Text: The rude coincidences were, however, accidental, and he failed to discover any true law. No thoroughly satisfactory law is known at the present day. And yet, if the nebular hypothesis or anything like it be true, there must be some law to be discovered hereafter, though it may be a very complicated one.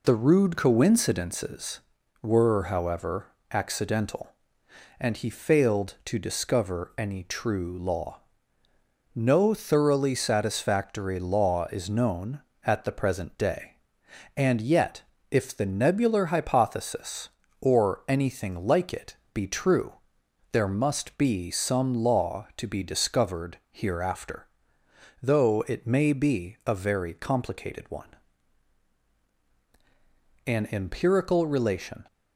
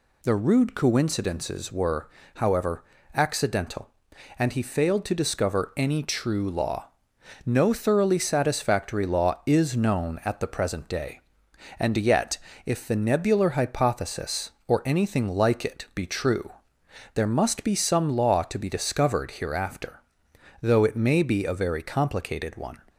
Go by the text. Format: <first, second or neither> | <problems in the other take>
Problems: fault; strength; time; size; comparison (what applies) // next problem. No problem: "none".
second | pauses between "it" and "be"; slight; at 19.1 s; 0.18 s long // goes on to say "An empirical relation"; from 30.4 s on; 1.5 s long